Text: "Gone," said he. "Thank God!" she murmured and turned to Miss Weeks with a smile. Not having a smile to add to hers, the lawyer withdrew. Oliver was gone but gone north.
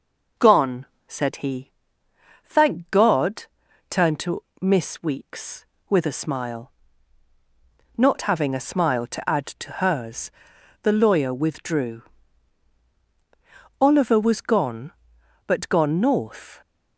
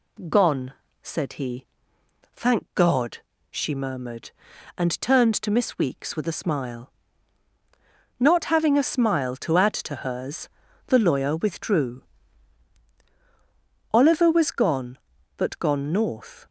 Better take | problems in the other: second | skips "she murmured and"; at 3.6 s // pauses between "to" and "Miss"; slight; at 4.4 s; 0.18 s long

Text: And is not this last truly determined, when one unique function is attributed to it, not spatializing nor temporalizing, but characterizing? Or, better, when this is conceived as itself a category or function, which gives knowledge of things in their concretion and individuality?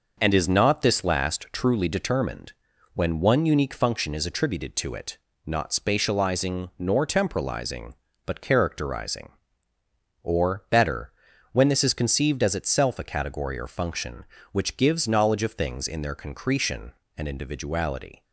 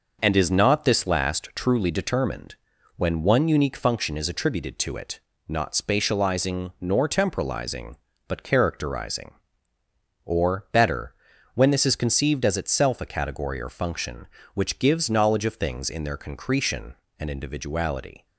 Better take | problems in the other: neither | none

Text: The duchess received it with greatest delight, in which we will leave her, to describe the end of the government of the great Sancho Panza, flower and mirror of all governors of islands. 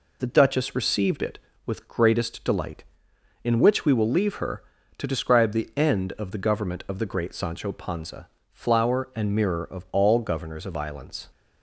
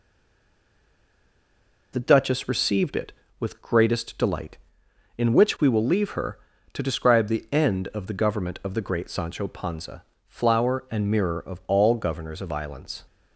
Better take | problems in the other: first | stays silent before the first word; noticeable; until 1.9 s; 1.9 s long

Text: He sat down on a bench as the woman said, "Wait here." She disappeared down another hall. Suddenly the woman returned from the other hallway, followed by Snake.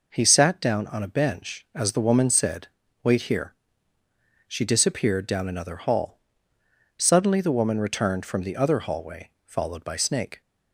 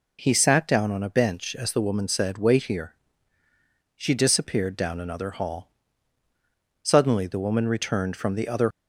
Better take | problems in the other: first | stops before "hallway followed by Snake"; at 8.7 s

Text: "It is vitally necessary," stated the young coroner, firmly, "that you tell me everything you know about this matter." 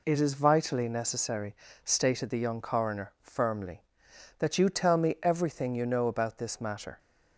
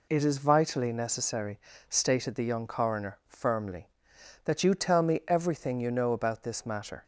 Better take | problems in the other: neither | none

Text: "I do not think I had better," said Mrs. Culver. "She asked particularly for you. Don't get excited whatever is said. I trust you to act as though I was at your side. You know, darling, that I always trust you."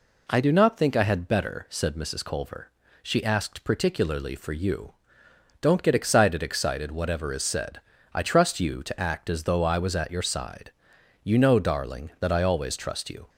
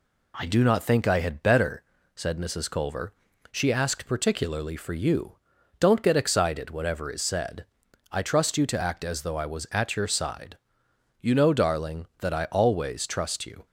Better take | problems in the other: second | says "excited" twice; at 6.4 s

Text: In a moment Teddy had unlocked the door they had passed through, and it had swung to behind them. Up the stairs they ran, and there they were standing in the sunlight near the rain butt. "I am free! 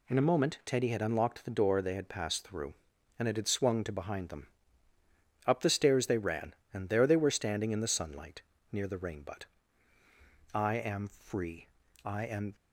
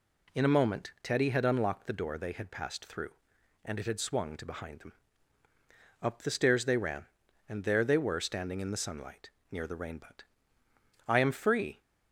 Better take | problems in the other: second | pauses between "sunlight" and "near"; slight; at 8.4 s; 0.28 s long; slight in the second // goes on to say "I am"; from 12.0 s on; 0.50 s long

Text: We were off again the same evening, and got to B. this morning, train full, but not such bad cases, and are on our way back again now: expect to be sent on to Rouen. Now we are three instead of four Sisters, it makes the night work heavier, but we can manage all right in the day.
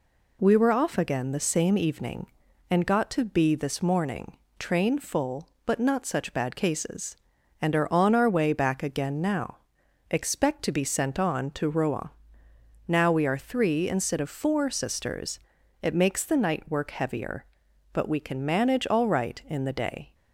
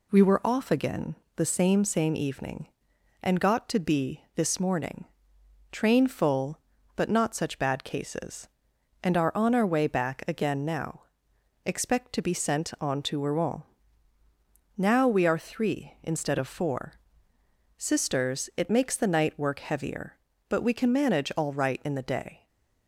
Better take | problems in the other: first | pauses between "again" and "the"; slight; at 1.1 s; 0.18 s long // says "same" twice; at 1.8 s // pauses between "four" and "Sisters"; noticeable; at 16.9 s; 0.84 s long // stays silent after the last word; slight; from 22.3 s on; 0.5 s long

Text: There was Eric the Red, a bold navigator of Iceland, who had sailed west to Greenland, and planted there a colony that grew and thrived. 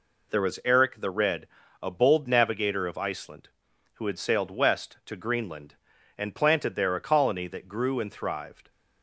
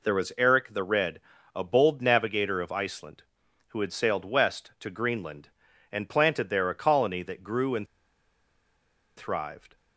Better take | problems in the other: first | pauses between "and" and "thrived"; strong; at 7.8 s; 1.3 s long

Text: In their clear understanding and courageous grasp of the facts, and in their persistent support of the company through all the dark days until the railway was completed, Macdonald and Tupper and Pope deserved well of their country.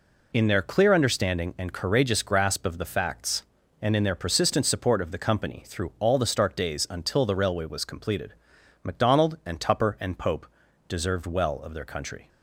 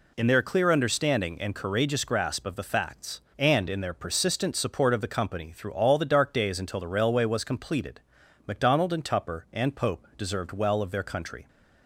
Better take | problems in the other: second | says "stark" for "dark"; at 6.2 s // pauses between "Pope" and "deserved"; at 10.4 s; 0.42 s long

